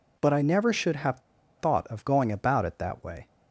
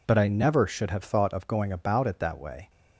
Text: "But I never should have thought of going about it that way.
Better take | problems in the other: second | pauses between "have" and "thought"; at 1.1 s; 0.39 s long

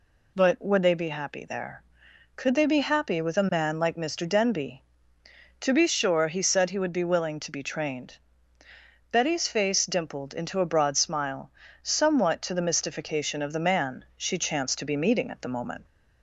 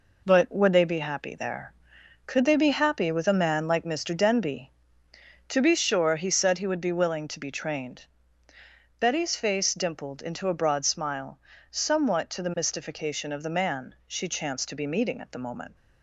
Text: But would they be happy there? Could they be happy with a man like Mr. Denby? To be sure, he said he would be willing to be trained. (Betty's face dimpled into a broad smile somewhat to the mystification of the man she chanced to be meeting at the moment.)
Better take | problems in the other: first | gets quieter; strong; throughout; 7.5 dB // pauses between "smile" and "somewhat"; slight; at 11.3 s; 0.32 s long; slight in the first

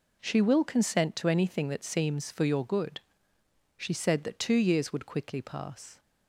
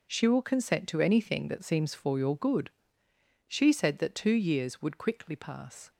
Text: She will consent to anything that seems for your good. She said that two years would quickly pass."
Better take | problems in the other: neither | none

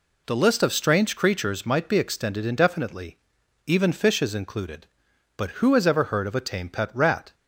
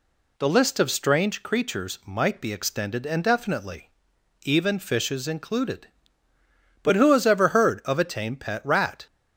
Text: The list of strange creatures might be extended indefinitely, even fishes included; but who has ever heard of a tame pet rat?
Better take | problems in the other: neither | none

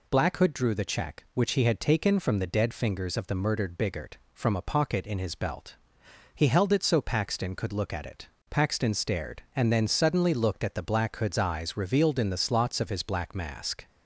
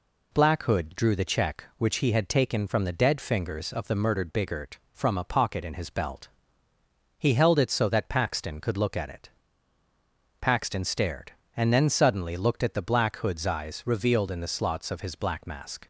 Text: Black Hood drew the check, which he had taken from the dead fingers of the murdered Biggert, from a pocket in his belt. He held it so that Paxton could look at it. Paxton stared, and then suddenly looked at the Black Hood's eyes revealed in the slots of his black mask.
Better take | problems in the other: second | skips "that"; at 7.0 s

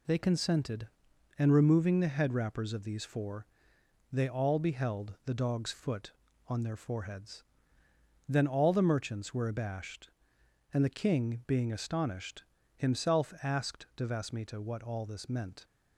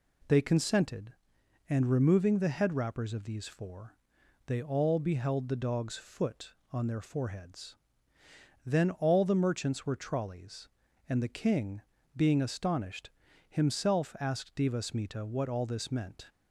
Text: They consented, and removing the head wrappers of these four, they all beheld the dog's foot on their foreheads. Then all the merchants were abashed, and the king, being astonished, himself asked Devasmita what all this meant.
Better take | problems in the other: first | says "trolleys" for "abashed"; at 9.9 s

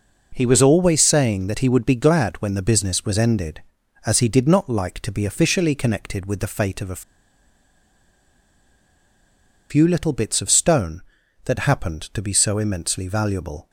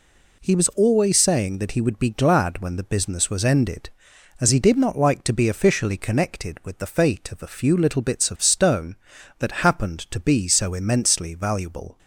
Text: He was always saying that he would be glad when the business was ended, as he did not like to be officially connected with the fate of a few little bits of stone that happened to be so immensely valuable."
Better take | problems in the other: second | pauses between "a" and "few"; strong; at 7.0 s; 2.6 s long

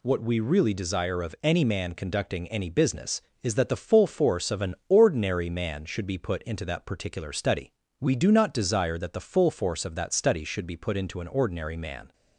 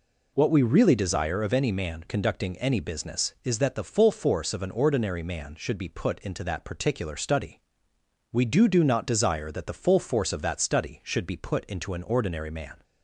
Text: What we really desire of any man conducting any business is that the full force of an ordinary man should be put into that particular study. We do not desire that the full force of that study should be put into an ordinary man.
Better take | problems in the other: first | says "do" twice; at 8.6 s

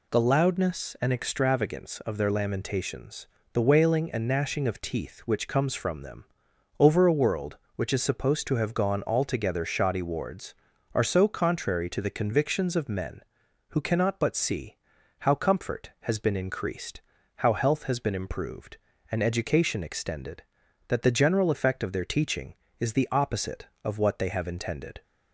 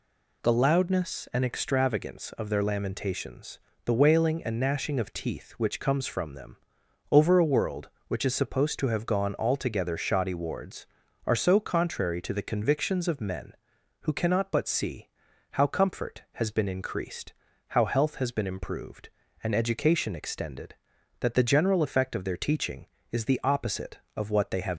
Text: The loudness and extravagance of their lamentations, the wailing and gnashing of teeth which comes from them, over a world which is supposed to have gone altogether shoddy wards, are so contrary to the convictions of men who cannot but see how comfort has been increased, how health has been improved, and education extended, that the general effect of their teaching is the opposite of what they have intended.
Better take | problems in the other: first | pauses between "see" and "how"; at 15.0 s; 0.42 s long; also in the first // stops before "intended"; at 24.7 s

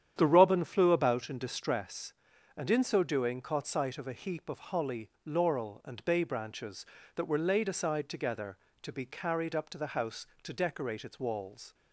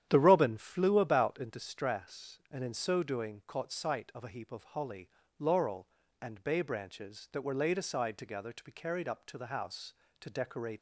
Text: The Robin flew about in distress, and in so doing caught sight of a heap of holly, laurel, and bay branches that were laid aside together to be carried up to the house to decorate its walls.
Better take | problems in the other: first | starts louder than the rest; strong; until 1.1 s; 10.5 dB; strong in the first // stops before "its walls"; at 10.7 s

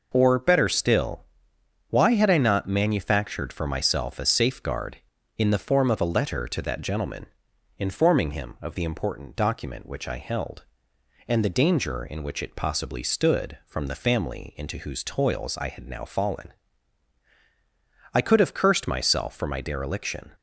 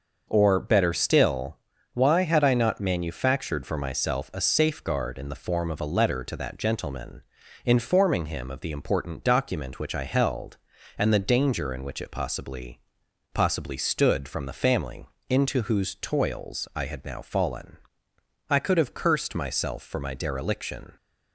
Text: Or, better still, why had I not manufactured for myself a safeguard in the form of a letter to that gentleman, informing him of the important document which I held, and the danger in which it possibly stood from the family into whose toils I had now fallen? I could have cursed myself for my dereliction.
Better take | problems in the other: first | starts louder than the rest; noticeable; until 1.3 s; 6 dB // says "possibly" twice; at 13.3 s // pauses between "family" and "into"; slight; at 15.0 s; 0.24 s long

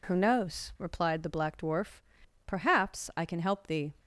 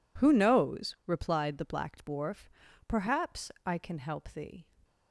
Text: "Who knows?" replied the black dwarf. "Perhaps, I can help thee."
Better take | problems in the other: neither | none

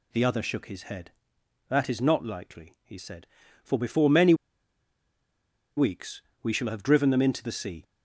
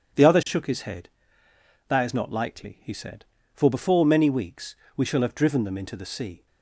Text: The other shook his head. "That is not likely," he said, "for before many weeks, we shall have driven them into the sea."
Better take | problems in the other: second | pauses between "many" and "weeks"; strong; at 4.3 s; 1.4 s long

